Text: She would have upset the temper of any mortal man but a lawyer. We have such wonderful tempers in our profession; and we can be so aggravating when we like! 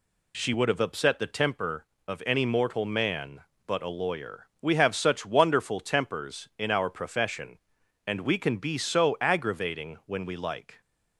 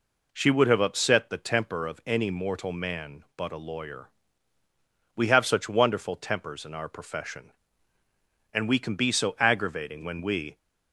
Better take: first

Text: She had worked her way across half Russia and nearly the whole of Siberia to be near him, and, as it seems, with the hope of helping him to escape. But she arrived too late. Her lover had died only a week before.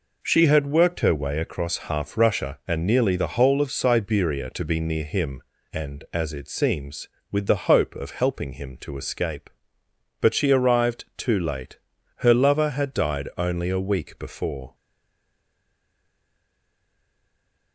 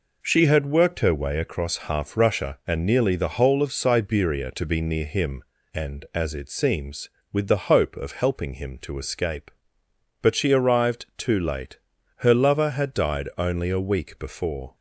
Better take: second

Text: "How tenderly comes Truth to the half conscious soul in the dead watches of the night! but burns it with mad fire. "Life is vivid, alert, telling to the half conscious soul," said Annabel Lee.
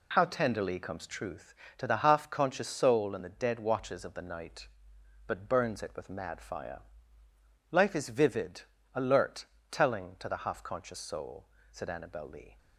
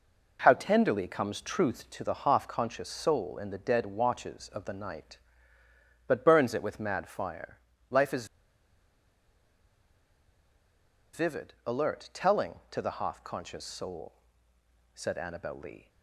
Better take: first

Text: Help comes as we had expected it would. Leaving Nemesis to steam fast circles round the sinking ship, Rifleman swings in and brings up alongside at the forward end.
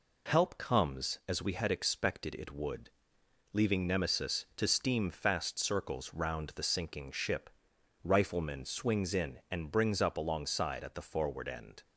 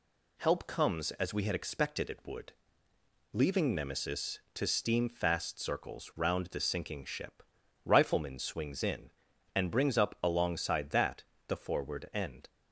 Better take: first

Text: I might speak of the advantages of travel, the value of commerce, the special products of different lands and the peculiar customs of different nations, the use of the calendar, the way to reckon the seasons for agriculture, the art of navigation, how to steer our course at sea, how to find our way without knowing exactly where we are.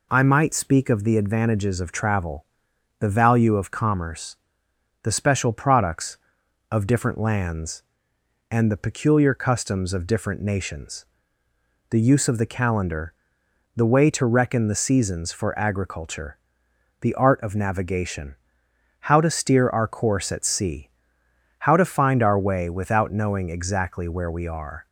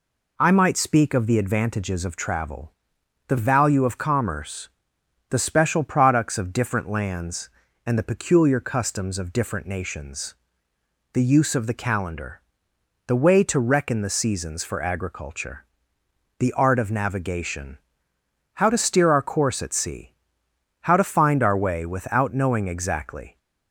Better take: first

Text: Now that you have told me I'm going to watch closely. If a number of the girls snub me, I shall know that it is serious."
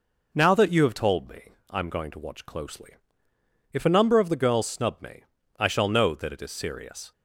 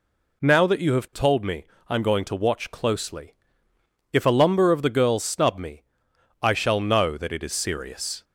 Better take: first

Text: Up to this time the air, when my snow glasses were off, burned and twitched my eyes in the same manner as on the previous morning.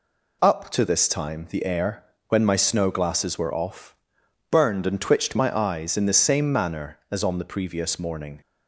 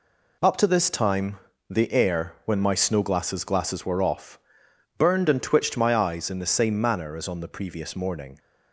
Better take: first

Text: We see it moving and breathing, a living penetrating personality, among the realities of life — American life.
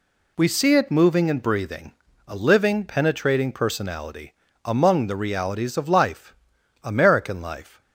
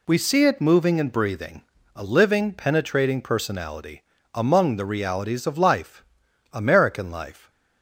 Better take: neither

